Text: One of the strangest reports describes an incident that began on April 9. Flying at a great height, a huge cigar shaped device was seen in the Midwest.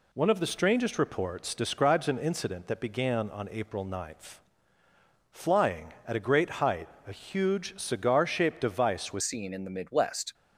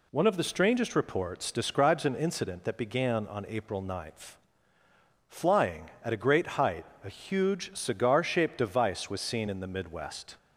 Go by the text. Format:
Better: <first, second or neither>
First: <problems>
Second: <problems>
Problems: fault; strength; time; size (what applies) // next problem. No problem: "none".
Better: second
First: changes voice at "seen"; from 9.2 s on; 1.1 s long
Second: none